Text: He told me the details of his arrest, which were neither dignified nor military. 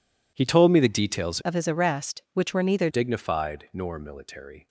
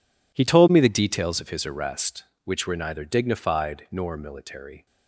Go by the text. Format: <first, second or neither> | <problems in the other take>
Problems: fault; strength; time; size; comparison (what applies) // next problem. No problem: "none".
second | changes voice from "of" to "neither"; from 1.4 to 2.8 s; 1.4 s long